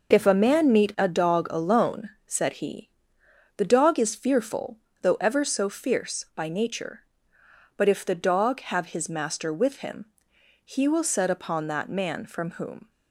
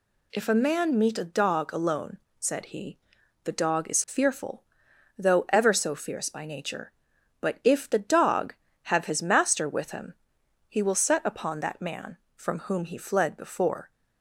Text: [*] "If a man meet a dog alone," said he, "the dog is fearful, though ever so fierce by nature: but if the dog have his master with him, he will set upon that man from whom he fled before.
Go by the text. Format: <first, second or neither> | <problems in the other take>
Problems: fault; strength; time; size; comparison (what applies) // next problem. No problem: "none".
second | stops before "he fled before"; at 12.8 s